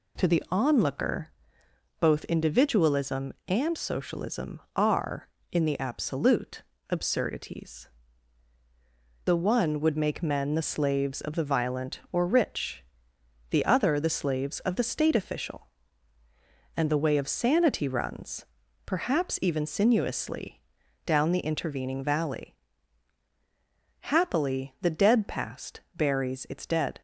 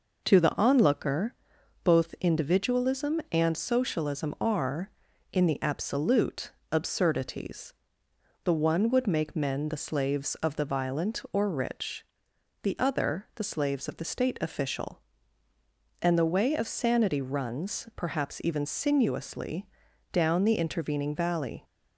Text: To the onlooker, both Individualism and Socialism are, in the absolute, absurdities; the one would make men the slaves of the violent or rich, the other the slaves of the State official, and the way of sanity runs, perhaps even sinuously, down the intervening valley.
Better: second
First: goes on to say "Happily the dead past buries its dead"; strong; from 24.0 s on; 3.0 s long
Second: none

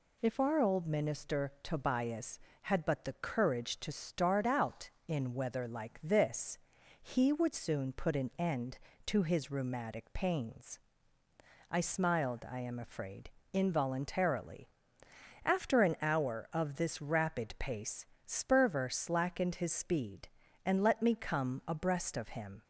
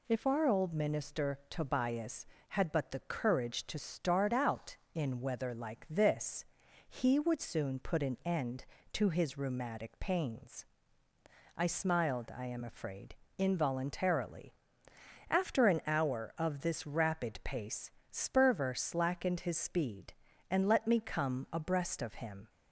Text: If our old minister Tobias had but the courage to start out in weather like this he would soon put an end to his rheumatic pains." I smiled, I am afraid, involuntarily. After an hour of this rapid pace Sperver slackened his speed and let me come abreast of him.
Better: neither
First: pauses between "this" and "he"; at 6.5 s; 0.42 s long // pauses between "pace" and "Sperver"; slight; at 18.0 s; 0.22 s long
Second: pauses between "this" and "he"; at 6.4 s; 0.42 s long // pauses between "pace" and "Sperver"; slight; at 17.8 s; 0.22 s long

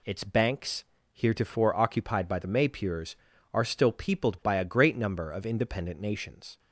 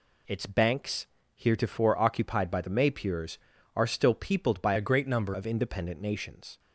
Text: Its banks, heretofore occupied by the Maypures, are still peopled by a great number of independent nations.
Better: first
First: none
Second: changes voice from "a" to "number"; from 4.7 to 5.3 s; 0.6 s long

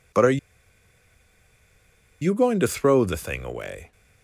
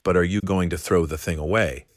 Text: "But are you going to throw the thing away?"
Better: second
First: pauses between "are" and "you"; strong; at 0.3 s; 1.8 s long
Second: none

